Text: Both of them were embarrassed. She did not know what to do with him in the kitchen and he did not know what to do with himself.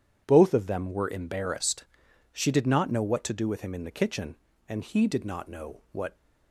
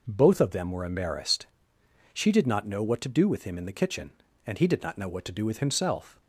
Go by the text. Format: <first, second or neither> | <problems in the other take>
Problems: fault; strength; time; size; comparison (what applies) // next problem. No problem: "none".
second | starts louder than the rest; strong; until 1.2 s; 9 dB // stops before "to do with himself"; at 6.1 s